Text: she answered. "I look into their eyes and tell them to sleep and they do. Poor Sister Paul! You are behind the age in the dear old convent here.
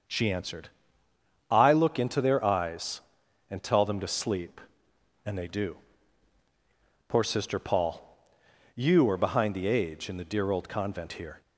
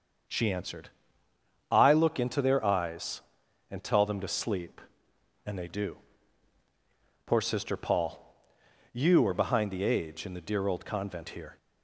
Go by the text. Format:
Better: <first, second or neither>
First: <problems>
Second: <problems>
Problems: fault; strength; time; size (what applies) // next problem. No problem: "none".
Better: neither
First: starts louder than the rest; until 1.9 s; 6.5 dB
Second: starts louder than the rest; until 2.1 s; 7 dB